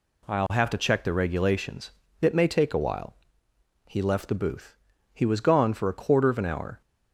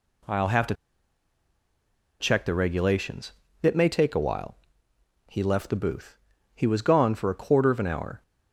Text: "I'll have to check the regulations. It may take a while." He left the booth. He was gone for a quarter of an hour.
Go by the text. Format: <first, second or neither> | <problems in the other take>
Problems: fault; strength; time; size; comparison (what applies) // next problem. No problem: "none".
first | pauses between "to" and "check"; strong; at 0.7 s; 1.4 s long